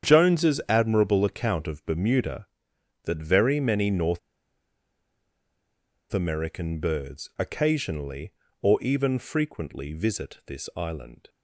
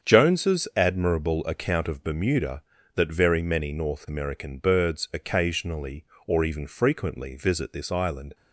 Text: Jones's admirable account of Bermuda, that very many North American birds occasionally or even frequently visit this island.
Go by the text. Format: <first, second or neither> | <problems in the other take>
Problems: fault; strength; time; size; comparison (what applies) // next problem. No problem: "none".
second | starts louder than the rest; strong; until 1.1 s; 8.5 dB; strong in the second // pauses between "North" and "American"; strong; at 4.1 s; 1.9 s long